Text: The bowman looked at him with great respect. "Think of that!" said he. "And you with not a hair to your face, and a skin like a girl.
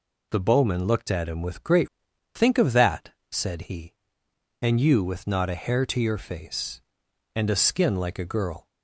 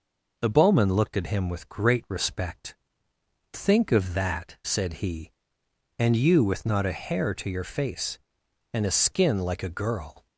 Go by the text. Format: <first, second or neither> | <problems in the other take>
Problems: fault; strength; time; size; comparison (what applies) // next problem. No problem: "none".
second | skips "respect"; at 2.1 s